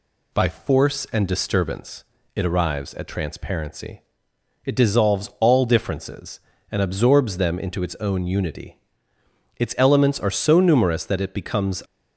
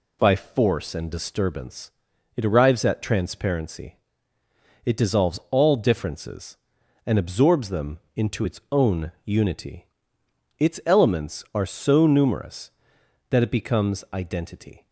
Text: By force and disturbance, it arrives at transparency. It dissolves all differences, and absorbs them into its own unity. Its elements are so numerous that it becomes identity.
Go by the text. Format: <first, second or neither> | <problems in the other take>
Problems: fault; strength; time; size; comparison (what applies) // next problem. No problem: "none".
second | stops before "identity"; at 11.8 s